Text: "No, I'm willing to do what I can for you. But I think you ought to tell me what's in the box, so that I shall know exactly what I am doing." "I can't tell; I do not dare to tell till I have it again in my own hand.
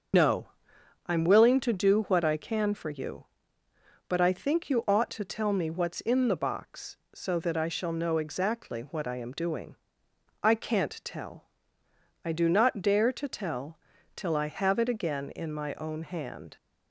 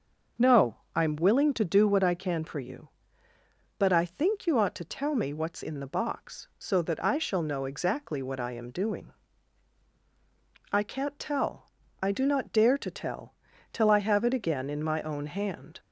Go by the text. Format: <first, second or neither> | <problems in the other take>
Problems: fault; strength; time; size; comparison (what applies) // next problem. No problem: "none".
second | loses the start of "No"; at 0.1 s; 80 ms // starts louder than the rest; until 1.7 s; 6.5 dB; also in the second // pauses between "tell" and "till"; at 13.7 s; 0.38 s long; also in the second